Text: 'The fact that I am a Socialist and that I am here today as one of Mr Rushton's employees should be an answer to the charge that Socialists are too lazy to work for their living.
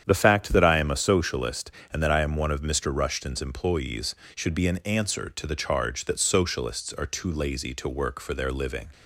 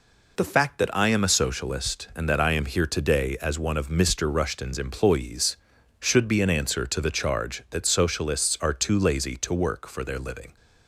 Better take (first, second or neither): second